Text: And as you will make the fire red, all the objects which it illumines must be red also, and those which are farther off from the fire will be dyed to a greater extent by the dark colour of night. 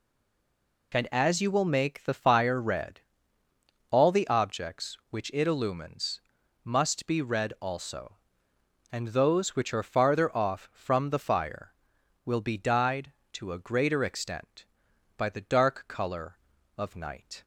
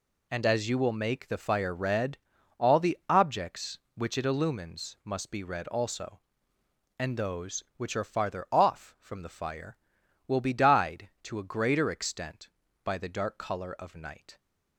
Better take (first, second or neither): second